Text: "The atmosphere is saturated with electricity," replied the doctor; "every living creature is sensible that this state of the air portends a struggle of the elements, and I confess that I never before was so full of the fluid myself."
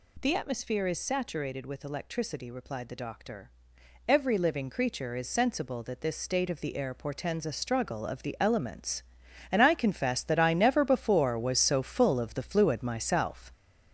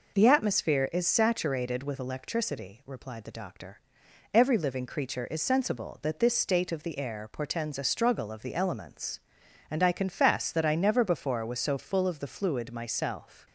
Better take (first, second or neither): second